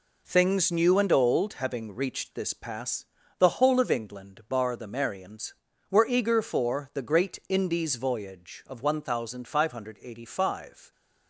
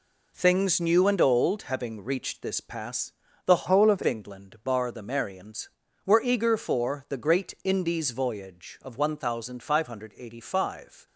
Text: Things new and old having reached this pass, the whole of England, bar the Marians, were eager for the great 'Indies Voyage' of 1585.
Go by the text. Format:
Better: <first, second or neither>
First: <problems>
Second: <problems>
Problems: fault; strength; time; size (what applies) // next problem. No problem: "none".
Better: first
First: none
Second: changes voice from "whole" to "of"; from 3.6 to 4.0 s; 0.4 s long